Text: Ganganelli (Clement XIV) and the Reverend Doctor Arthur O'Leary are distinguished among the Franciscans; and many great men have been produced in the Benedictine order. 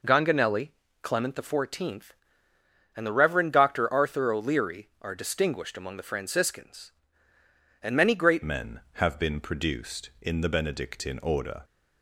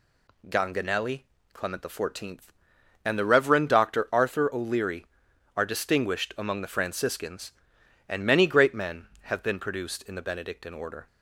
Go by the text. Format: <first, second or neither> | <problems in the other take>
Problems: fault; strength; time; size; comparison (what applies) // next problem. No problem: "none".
second | changes voice at "men"; from 8.4 s on; 3.2 s long